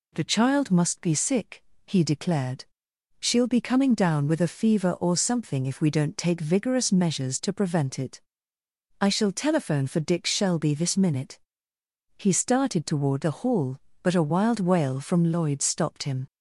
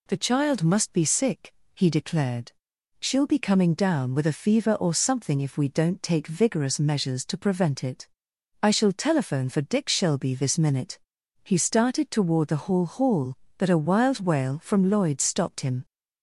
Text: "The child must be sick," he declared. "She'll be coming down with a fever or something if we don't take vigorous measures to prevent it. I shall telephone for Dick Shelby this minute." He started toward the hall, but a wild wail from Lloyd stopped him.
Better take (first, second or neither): first